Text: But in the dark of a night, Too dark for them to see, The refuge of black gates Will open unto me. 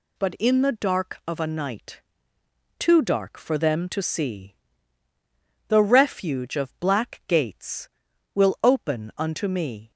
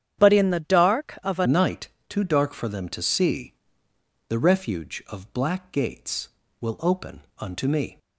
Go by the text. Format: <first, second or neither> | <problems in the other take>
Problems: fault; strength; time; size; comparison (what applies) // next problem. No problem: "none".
first | starts louder than the rest; strong; until 1.2 s; 9.5 dB // changes voice at "night"; from 1.4 s on; 6.5 s long // pauses between "open" and "unto"; slight; at 7.2 s; 0.16 s long